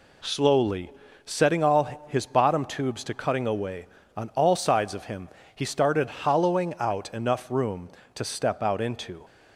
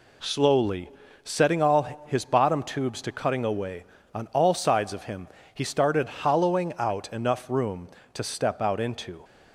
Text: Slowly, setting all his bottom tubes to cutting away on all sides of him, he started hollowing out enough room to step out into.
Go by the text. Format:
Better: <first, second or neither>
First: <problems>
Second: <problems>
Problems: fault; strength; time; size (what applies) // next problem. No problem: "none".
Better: neither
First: none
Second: none